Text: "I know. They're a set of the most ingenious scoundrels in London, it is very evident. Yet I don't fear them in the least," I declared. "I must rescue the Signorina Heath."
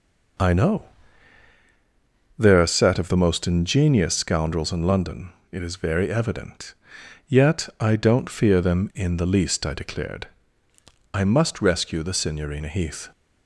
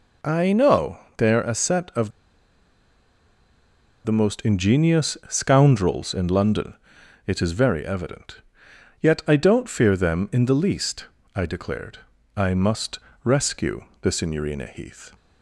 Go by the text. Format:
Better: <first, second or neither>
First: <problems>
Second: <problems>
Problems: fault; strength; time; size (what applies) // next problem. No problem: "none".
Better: first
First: none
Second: pauses between "of" and "the"; strong; at 2.1 s; 1.9 s long // pauses between "must" and "rescue"; slight; at 12.9 s; 0.24 s long // pauses between "rescue" and "the"; slight; at 13.8 s; 0.18 s long